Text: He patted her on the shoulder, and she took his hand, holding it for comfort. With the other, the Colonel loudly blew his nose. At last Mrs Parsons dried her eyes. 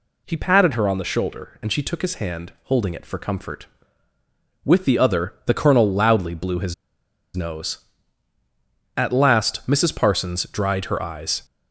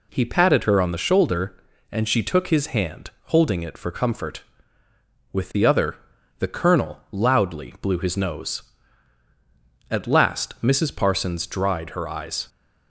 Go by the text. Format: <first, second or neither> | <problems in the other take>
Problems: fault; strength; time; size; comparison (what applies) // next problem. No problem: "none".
second | pauses between "his" and "nose"; noticeable; at 6.7 s; 0.60 s long